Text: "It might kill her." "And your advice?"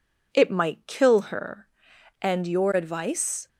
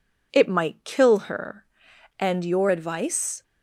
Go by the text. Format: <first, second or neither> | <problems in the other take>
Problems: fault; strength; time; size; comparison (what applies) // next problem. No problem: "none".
neither | none